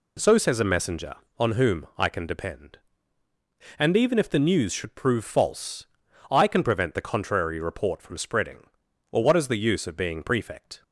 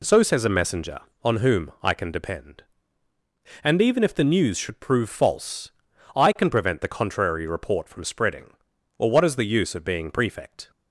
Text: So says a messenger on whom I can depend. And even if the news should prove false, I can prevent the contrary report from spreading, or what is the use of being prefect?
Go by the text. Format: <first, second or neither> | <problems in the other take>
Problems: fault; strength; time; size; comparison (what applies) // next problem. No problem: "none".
neither | none